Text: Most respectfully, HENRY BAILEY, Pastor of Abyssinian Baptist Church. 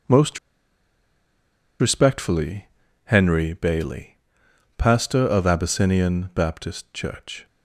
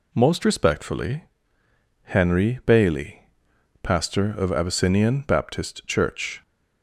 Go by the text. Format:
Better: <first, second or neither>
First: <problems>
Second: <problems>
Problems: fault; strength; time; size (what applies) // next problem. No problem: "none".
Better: second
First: pauses between "Most" and "respectfully"; strong; at 0.3 s; 1.4 s long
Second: none